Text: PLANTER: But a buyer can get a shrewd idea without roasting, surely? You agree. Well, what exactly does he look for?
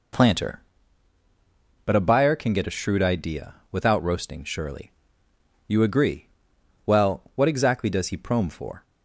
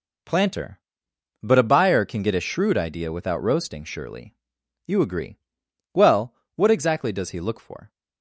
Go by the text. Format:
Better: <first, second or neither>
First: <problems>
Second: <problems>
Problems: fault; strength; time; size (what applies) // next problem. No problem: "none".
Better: second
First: pauses between "idea" and "without"; slight; at 3.5 s; 0.18 s long // says "prome" for "look"; at 8.1 s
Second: none